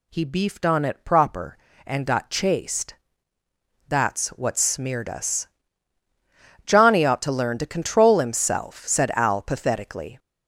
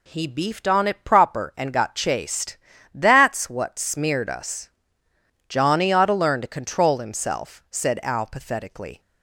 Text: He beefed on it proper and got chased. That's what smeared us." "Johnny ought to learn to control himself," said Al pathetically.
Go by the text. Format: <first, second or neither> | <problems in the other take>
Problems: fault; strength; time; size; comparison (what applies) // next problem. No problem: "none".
neither | none